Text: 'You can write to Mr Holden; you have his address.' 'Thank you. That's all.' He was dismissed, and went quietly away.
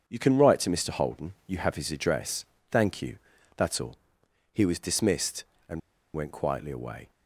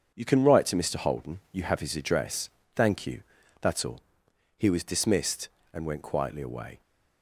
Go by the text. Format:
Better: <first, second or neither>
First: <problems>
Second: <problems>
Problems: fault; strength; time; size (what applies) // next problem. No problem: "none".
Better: second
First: starts louder than the rest; strong; until 1.0 s; 7 dB // pauses between "and" and "went"; slight; at 5.8 s; 0.34 s long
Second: starts louder than the rest; until 1.1 s; 7 dB